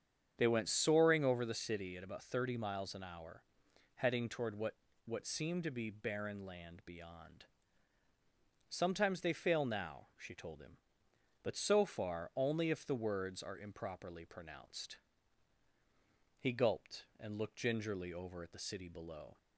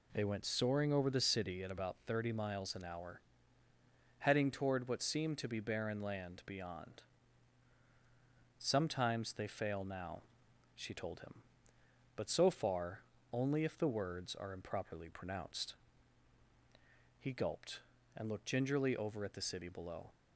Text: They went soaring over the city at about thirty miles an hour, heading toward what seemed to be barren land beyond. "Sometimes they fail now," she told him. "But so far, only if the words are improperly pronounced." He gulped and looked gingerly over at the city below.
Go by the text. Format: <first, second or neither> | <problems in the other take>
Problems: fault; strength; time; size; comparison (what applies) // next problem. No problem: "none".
second | starts louder than the rest; strong; until 1.3 s; 8 dB // says "what" twice; at 5.0 s